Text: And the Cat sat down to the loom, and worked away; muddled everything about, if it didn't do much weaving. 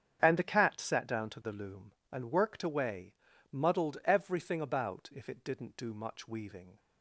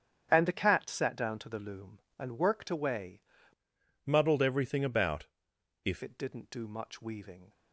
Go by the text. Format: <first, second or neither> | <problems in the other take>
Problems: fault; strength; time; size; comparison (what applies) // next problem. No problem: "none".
first | starts louder than the rest; strong; until 1.3 s; 8 dB; strong in the first // changes voice from "muddled" to "if"; from 4.0 to 6.0 s; 2.0 s long